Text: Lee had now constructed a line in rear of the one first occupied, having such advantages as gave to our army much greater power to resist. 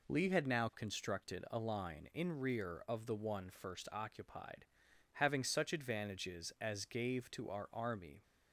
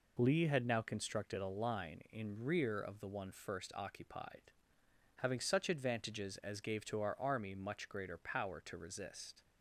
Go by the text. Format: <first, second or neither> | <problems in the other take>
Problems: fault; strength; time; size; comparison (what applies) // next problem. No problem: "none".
second | stops before "much greater power to resist"; at 8.2 s